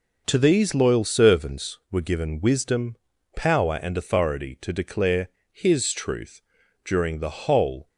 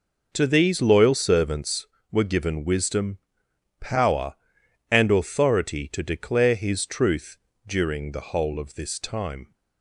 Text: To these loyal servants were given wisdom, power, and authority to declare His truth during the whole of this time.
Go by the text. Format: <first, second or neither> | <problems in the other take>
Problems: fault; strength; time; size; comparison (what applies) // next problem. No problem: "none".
second | pauses between "declare" and "His"; slight; at 5.2 s; 0.24 s long // pauses between "truth" and "during"; at 6.4 s; 0.44 s long; slight in the second // stops before "of this time"; at 7.8 s